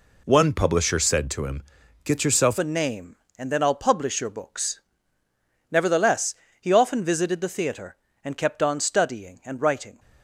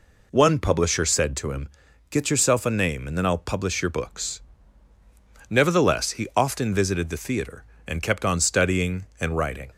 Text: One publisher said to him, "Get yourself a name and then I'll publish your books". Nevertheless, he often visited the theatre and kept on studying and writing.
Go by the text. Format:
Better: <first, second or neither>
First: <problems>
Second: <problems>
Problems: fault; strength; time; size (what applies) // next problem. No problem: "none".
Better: second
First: changes voice at "a"; from 2.5 s on; 7.4 s long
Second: none